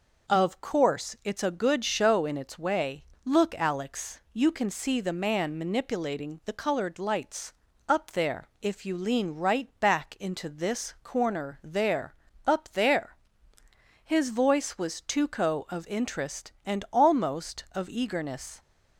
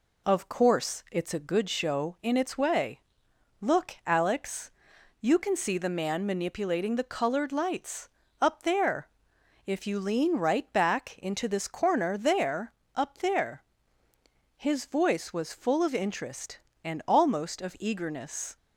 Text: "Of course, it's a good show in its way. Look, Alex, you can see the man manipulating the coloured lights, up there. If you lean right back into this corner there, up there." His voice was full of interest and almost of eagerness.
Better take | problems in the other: second | says "tuco" for "full"; at 15.0 s

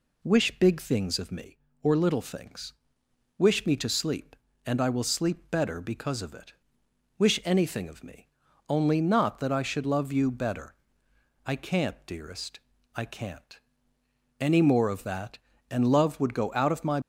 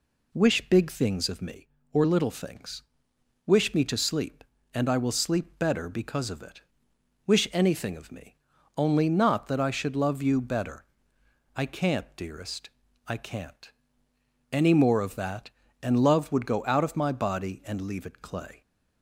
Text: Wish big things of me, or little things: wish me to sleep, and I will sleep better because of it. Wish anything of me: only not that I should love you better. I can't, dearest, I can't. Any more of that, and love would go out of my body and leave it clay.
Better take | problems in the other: second | stops before "body and leave it clay"; at 17.0 s

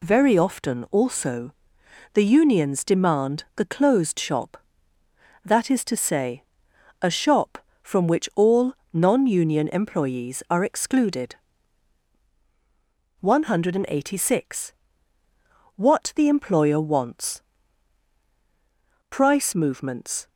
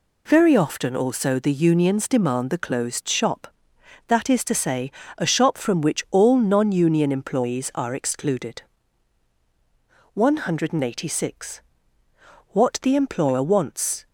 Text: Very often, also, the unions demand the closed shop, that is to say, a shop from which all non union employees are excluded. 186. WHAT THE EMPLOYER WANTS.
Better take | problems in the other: second | pauses between "all" and "non"; slight; at 8.7 s; 0.18 s long // goes on to say "Price movements"; noticeable; from 19.1 s on; 1.1 s long

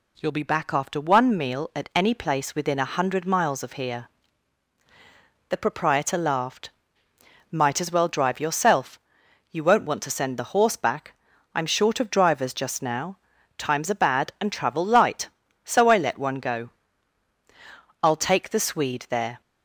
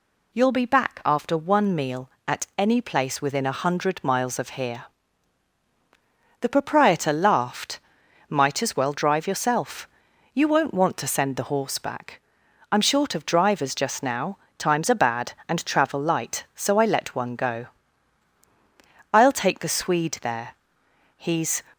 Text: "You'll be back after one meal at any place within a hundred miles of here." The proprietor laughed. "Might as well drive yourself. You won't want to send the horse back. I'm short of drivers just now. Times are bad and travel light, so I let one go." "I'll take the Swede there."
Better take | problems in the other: first | goes on to say "He's"; slight; from 21.1 s on; 0.44 s long

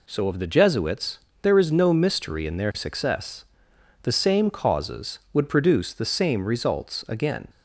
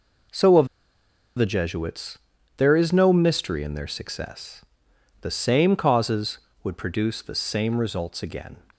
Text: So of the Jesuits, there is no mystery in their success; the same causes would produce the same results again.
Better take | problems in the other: first | pauses between "of" and "the"; noticeable; at 0.6 s; 0.70 s long

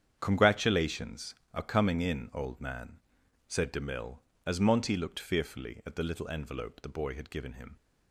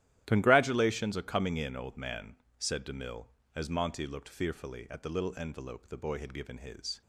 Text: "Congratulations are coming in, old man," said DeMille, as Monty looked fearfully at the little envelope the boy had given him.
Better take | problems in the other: first | starts louder than the rest; strong; until 1.2 s; 12.5 dB; strong in the first // says "his" for "him"; at 6.5 s

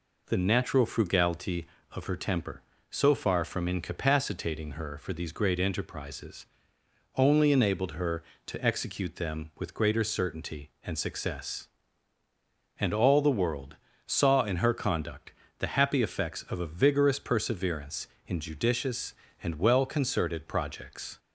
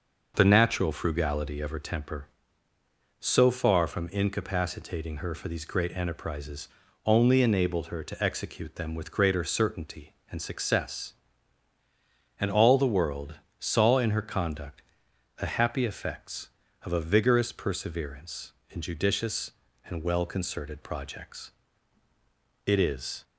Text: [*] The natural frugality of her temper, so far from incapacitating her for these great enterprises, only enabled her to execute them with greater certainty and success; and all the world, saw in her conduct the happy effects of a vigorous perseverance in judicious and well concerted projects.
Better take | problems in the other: first | pauses between "conduct" and "the"; noticeable; at 14.8 s; 0.56 s long; slight in the first // goes on to say "It is"; from 22.6 s on; 0.58 s long

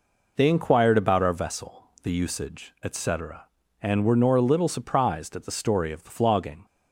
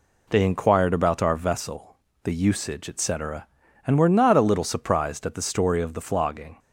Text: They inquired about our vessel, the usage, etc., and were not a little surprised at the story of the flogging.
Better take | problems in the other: second | says "nor" for "not"; at 4.1 s

